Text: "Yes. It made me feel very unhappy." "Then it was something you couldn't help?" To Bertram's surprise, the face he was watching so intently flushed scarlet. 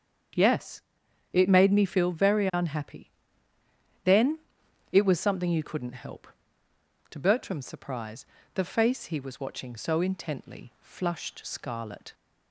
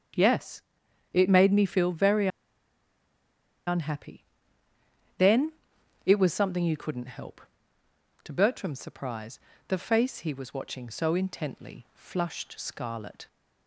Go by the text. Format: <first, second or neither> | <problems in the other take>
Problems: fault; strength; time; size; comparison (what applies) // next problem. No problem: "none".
first | starts louder than the rest; strong; until 1.6 s; 8 dB; strong in the first // pauses between "very" and "unhappy"; strong; at 2.2 s; 1.3 s long // pauses between "Then" and "it"; noticeable; at 5.5 s; 0.54 s long; noticeable in the first